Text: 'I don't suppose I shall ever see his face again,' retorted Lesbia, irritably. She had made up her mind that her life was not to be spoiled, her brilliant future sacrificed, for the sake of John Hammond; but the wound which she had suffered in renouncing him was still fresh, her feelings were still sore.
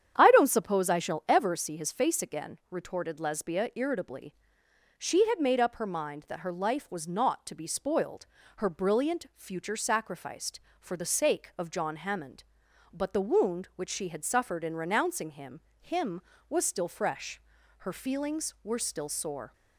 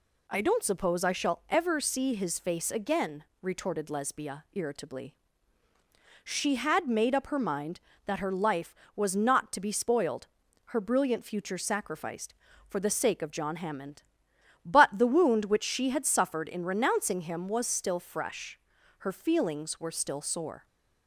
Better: second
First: starts louder than the rest; strong; until 1.1 s; 9 dB // says "him" twice; at 15.8 s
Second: none

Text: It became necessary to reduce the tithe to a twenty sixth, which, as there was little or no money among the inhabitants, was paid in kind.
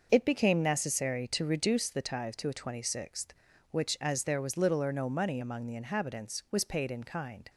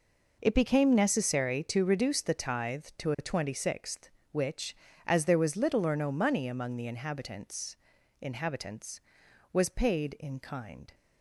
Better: first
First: none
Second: says "inhabitants" twice; at 8.2 s

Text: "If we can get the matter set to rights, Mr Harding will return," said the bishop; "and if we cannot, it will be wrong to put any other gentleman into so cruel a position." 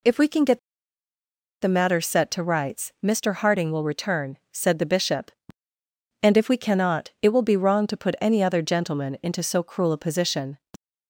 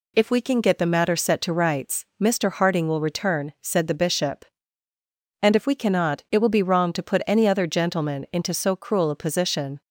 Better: second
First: pauses between "get" and "the"; at 0.5 s; 1.0 s long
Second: none

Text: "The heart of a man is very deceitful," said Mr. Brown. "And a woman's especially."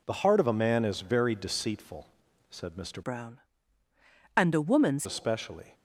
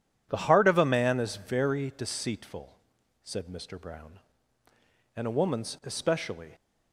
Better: second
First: changes voice from "Brown" to "woman's"; from 3.0 to 5.0 s; 2.0 s long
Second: none

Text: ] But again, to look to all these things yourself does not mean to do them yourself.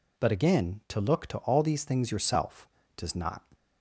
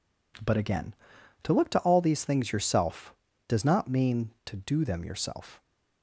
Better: second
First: stops before "mean to do them yourself"; at 3.5 s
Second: none

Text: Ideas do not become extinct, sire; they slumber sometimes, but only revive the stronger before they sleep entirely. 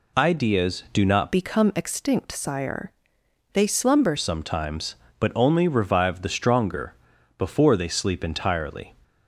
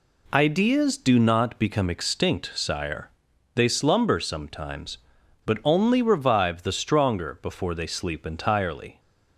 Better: second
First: changes voice from "become" to "slumber"; from 1.3 to 4.1 s; 2.8 s long // pauses between "stronger" and "before"; noticeable; at 6.9 s; 0.46 s long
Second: none

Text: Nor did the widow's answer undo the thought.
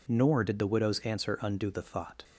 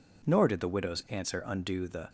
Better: first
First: none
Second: stops before "thought"; at 2.0 s

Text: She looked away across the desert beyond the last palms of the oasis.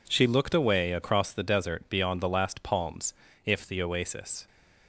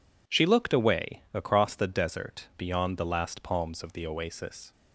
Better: second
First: says "if" for "of"; at 3.4 s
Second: none

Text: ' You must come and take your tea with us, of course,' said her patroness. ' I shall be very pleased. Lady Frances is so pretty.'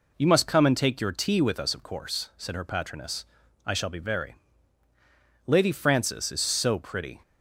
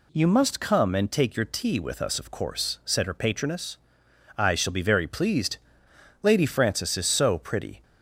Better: second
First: skips "pleased"; at 4.8 s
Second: none

